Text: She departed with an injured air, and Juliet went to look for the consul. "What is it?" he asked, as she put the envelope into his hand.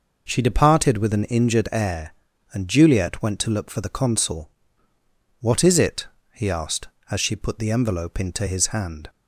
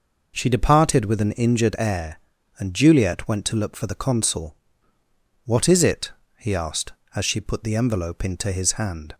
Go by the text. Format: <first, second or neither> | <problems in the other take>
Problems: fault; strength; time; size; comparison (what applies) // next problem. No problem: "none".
neither | none